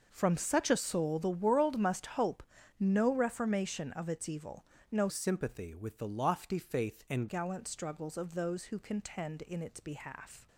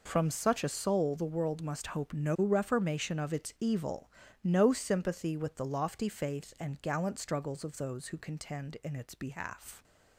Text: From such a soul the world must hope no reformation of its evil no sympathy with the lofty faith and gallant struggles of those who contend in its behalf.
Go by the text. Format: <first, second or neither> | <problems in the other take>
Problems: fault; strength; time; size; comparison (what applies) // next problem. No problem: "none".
second | pauses between "hope" and "no"; at 2.4 s; 0.38 s long // pauses between "evil" and "no"; slight; at 4.6 s; 0.26 s long; slight in the second // changes voice from "sympathy" to "and"; from 5.0 to 7.2 s; 2.2 s long